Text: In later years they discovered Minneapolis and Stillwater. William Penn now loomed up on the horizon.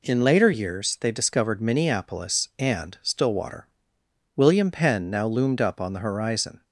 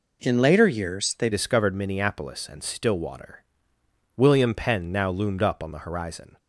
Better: first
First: none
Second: changes voice at "discovered"; from 1.3 s on; 5.0 s long

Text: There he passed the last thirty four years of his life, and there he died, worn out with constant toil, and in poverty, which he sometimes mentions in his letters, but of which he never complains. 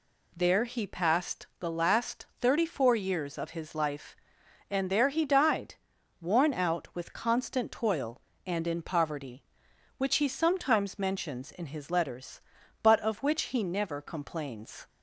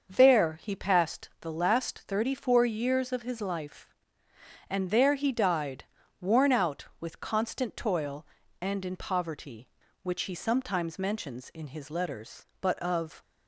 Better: first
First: none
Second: starts louder than the rest; until 1.1 s; 6 dB // stops before "which he never complains"; at 13.2 s

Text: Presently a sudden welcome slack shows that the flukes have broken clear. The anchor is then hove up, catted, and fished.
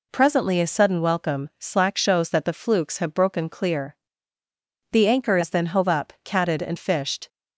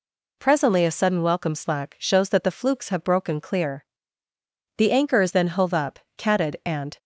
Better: first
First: none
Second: stops before "fished"; at 6.9 s

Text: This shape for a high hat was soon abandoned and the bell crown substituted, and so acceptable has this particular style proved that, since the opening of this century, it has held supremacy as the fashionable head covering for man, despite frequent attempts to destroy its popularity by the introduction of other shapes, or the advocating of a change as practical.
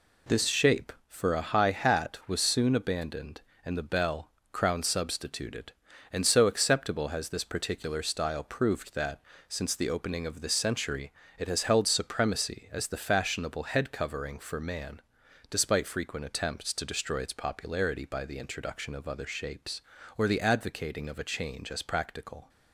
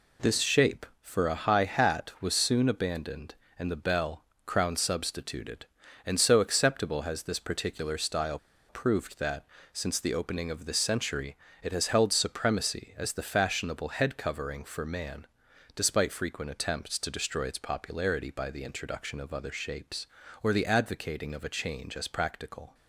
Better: first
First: pauses between "bell" and "crown"; slight; at 4.2 s; 0.22 s long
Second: pauses between "bell" and "crown"; slight; at 4.2 s; 0.22 s long // pauses between "style" and "proved"; slight; at 8.3 s; 0.31 s long

